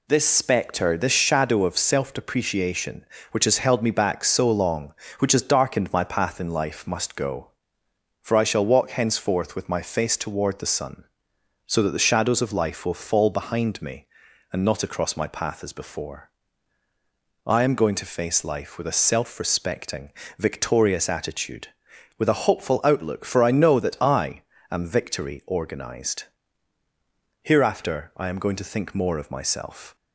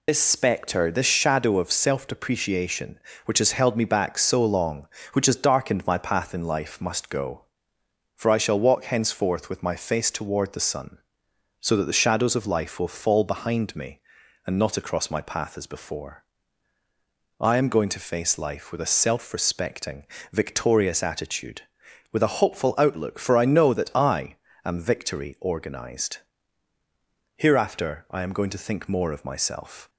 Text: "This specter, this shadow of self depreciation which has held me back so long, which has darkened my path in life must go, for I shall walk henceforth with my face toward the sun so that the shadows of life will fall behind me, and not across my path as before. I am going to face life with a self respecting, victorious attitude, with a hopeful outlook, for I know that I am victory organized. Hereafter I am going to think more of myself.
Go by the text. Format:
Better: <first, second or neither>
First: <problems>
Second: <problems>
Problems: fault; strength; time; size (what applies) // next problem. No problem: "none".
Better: first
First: pauses between "I" and "am"; slight; at 24.4 s; 0.28 s long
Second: loses the start of "This"; at 0.0 s; 55 ms // pauses between "I" and "am"; slight; at 24.3 s; 0.28 s long